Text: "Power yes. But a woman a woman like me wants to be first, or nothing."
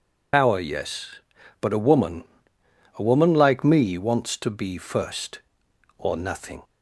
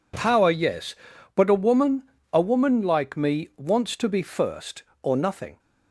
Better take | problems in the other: second | loses the start of "Power"; at 0.3 s; 75 ms // pauses between "woman" and "a"; noticeable; at 2.2 s; 0.72 s long; slight in the second

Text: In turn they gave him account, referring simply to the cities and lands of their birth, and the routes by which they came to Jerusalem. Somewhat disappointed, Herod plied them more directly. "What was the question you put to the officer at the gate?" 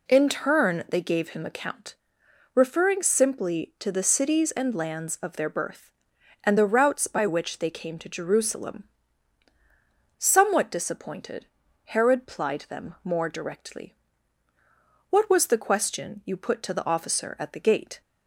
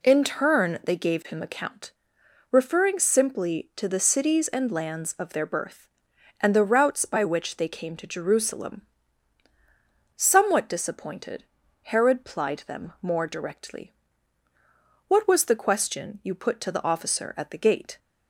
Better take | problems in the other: neither | none

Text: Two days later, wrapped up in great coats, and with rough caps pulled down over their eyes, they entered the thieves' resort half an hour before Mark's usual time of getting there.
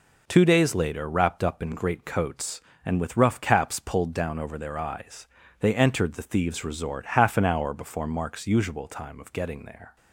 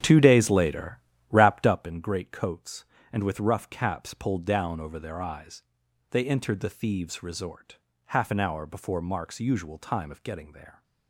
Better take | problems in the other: first | starts louder than the rest; strong; until 1.9 s; 9 dB // pauses between "resort" and "half"; slight; at 7.7 s; 0.30 s long

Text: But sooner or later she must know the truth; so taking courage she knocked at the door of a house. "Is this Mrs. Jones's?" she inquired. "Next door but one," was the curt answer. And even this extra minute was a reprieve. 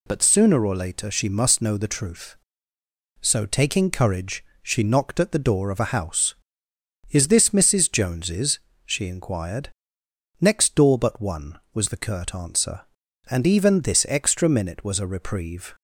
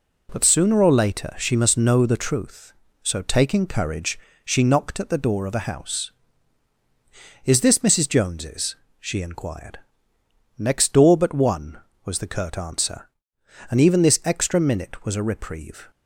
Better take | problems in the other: neither | pauses between "courage" and "she"; slight; the same in both

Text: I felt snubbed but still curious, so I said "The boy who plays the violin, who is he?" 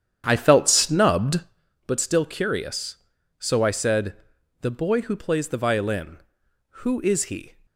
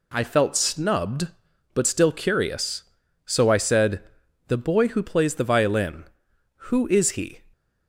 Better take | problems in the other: second | starts louder than the rest; strong; until 1.6 s; 9 dB // pauses between "said" and "The"; noticeable; at 4.1 s; 0.46 s long; noticeable in the second

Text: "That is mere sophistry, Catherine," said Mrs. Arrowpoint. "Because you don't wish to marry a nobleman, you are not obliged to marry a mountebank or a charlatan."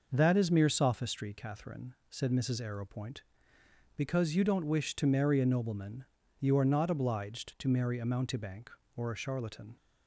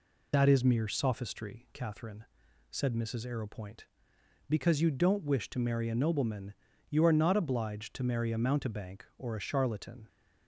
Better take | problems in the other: first | loses the start of "That"; at 0.3 s; 40 ms

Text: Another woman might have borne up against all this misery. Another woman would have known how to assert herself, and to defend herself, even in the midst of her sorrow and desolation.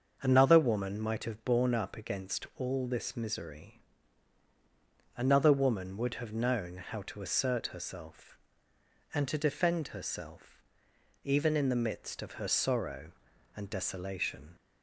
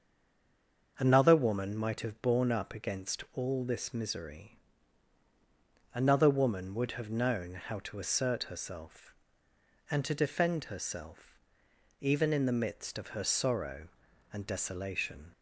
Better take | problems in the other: first | stays silent before the first word; slight; until 0.9 s; 0.9 s long // starts louder than the rest; until 2.0 s; 6.5 dB; also in the first

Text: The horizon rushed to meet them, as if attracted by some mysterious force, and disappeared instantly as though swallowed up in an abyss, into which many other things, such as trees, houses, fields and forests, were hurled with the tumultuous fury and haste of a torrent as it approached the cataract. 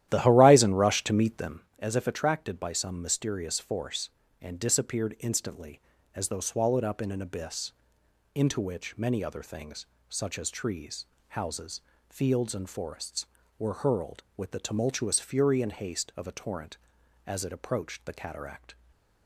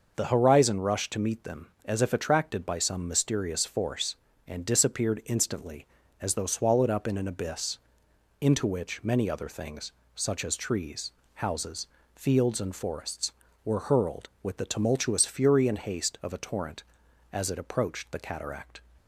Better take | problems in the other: second | starts louder than the rest; strong; until 1.7 s; 12.5 dB // stays silent after the last word; slight; from 18.7 s on; 0.5 s long

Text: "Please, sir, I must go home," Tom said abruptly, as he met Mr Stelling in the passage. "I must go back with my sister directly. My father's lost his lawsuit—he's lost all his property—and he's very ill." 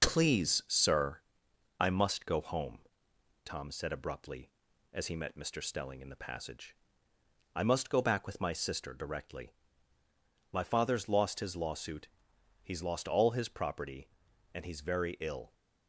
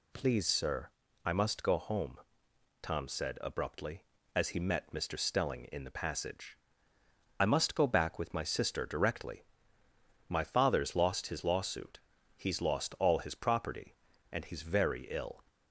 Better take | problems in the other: second | gets quieter; noticeable; throughout; 5 dB

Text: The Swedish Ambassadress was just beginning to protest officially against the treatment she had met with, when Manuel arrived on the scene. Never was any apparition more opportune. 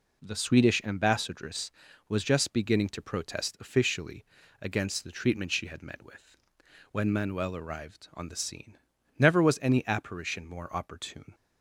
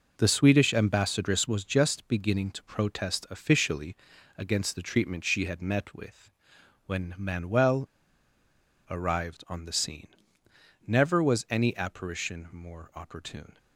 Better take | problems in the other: first | pauses between "officially" and "against"; at 3.9 s; 0.42 s long; also in the first // pauses between "Manuel" and "arrived"; at 7.8 s; 1.0 s long

